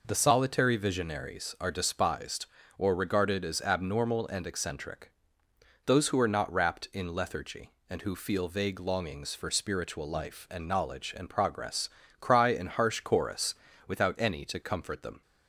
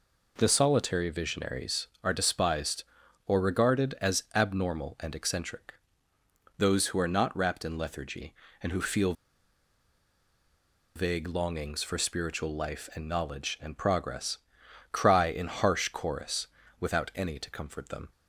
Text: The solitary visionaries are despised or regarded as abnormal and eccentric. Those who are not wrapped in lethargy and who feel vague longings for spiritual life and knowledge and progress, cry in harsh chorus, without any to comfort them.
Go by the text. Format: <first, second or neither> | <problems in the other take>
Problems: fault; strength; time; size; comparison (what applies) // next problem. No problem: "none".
first | pauses between "feel" and "vague"; strong; at 9.1 s; 1.8 s long